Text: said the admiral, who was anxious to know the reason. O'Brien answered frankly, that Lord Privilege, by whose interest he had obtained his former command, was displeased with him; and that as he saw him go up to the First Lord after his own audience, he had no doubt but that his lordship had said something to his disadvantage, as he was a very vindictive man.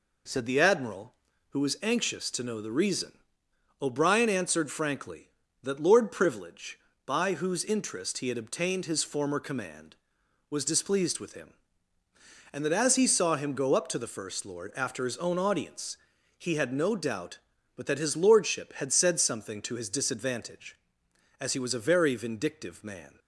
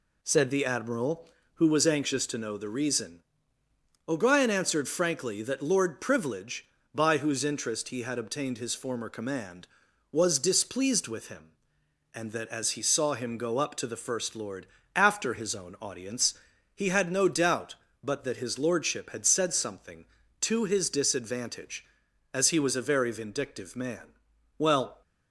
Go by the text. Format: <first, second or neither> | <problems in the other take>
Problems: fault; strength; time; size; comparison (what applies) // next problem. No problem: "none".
first | pauses between "Lord" and "after"; slight; at 14.6 s; 0.28 s long // goes on to say "Well"; slight; from 24.5 s on; 0.44 s long